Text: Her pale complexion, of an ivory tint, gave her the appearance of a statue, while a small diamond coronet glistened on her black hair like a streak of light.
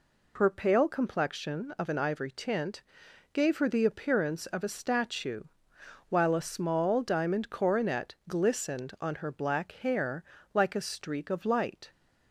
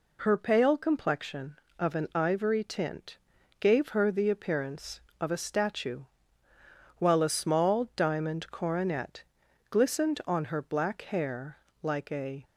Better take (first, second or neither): first